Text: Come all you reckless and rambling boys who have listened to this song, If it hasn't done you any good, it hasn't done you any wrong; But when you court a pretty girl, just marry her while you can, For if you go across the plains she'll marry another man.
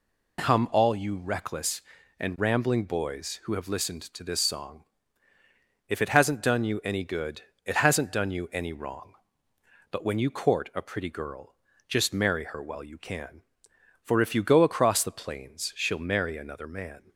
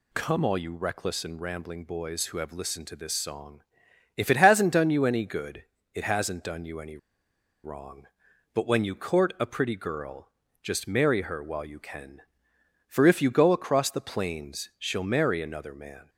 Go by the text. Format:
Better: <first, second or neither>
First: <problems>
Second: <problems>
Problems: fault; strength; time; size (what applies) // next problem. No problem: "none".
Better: first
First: none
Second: pauses between "any" and "wrong"; noticeable; at 6.9 s; 0.66 s long